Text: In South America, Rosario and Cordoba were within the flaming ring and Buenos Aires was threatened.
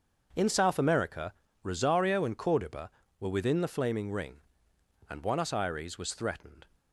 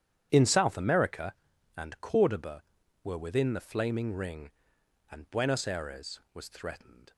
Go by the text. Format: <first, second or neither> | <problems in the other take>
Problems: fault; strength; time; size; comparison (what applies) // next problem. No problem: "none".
first | starts louder than the rest; strong; until 1.3 s; 9.5 dB; also in the first // skips "Rosario"; at 1.5 s